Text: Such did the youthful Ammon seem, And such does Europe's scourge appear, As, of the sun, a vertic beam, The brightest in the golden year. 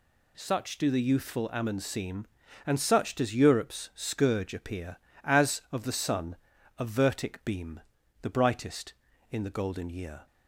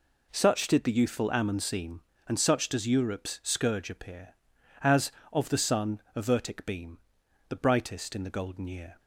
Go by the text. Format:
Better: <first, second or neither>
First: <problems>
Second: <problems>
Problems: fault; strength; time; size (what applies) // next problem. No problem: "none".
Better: second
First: says "do" for "did"; at 0.7 s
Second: none